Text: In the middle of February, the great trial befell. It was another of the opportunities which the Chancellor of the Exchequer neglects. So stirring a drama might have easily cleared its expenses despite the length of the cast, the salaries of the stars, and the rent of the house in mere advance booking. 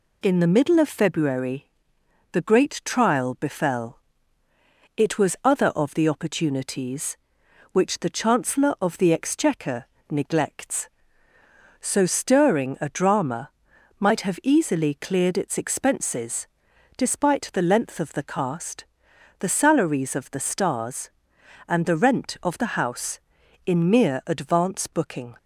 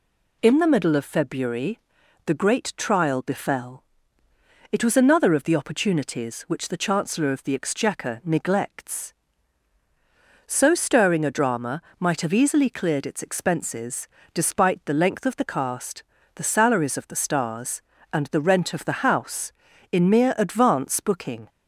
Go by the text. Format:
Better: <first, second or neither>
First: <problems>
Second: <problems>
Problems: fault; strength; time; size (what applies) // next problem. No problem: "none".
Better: second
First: says "other" for "another"; at 5.4 s // pauses between "Exchequer" and "neglects"; slight; at 9.8 s; 0.26 s long // pauses between "drama" and "might"; noticeable; at 13.4 s; 0.48 s long // pauses between "expenses" and "despite"; noticeable; at 16.4 s; 0.52 s long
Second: pauses between "drama" and "might"; slight; at 11.8 s; 0.18 s long // pauses between "expenses" and "despite"; slight; at 14.0 s; 0.26 s long